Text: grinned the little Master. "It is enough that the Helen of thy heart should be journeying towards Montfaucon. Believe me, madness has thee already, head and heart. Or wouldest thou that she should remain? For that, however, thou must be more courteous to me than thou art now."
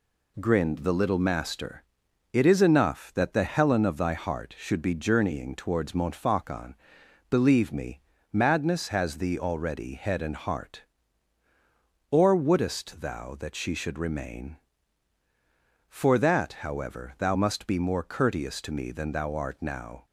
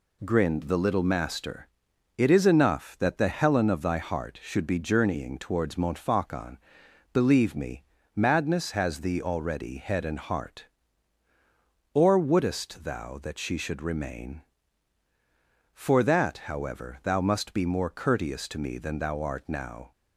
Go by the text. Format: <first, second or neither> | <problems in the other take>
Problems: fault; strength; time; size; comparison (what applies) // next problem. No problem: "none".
neither | none